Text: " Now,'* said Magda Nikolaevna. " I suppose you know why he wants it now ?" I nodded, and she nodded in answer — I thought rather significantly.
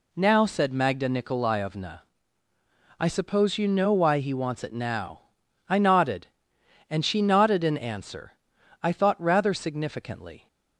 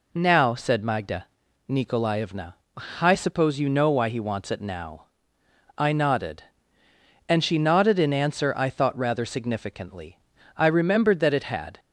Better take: first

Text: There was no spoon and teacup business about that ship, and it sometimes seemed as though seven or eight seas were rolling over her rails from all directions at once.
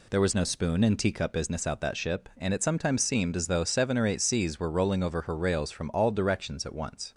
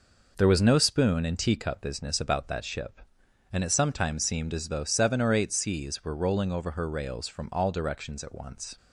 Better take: second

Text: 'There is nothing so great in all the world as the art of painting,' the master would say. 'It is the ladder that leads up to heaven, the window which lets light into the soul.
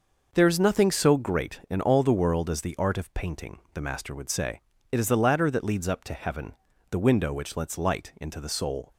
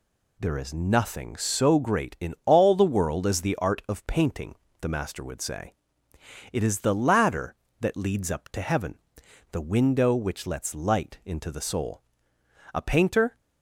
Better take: first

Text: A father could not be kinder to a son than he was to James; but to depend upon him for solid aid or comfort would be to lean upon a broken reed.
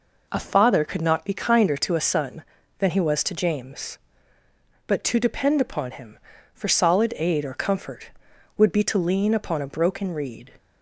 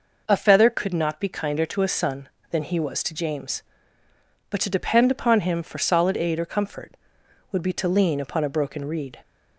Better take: first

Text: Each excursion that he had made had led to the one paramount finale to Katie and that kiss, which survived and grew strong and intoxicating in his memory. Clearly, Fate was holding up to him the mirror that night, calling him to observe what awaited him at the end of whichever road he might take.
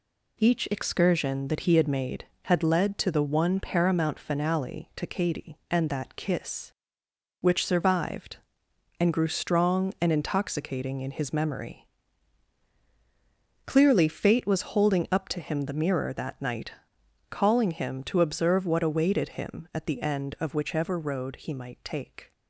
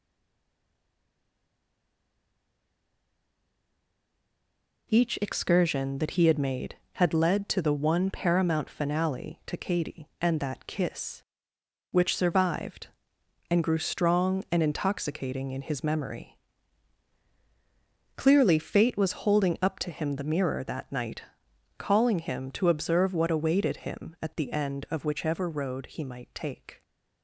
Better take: first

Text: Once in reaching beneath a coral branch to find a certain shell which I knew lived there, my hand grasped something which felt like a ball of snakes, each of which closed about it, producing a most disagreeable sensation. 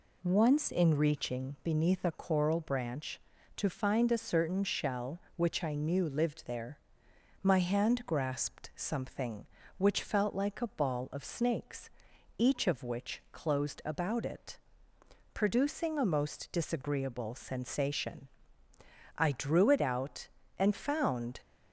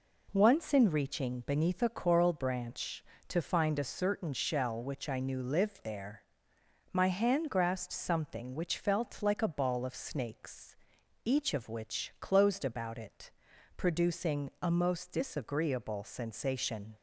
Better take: second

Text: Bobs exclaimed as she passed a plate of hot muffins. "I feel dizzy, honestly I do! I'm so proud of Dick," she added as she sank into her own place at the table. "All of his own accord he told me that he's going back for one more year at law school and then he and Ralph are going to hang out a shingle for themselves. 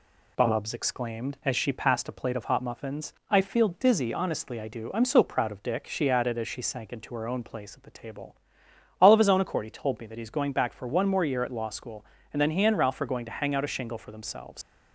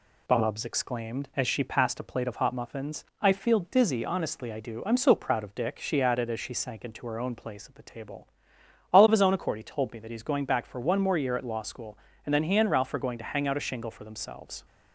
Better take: second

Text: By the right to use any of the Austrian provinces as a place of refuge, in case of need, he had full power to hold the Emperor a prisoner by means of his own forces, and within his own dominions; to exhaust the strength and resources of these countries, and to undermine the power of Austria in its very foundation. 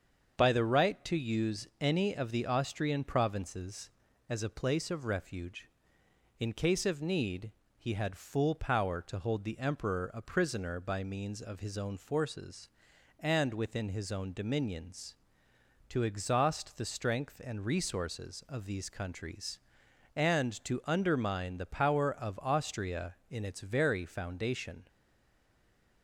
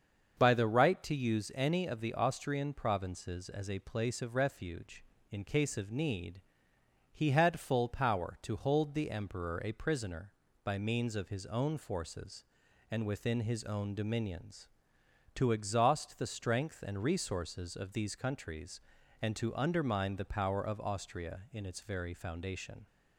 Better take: second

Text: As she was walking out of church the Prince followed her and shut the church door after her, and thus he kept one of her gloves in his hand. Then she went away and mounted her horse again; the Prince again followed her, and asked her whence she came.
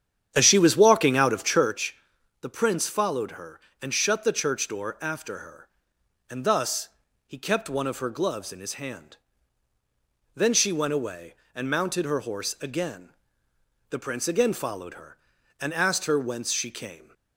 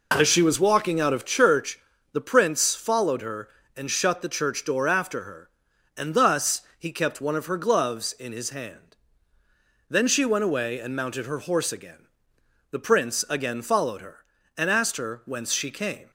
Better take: second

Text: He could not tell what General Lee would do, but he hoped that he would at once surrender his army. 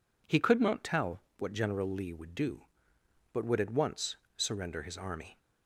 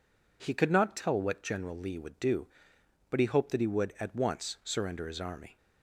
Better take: second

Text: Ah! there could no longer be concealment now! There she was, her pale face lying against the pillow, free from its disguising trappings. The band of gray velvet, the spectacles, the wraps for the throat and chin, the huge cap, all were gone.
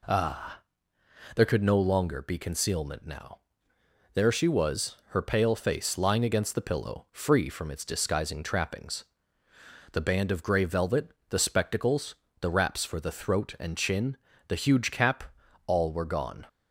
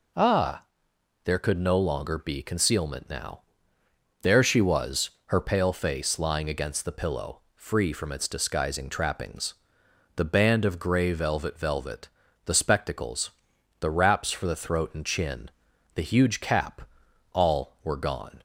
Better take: first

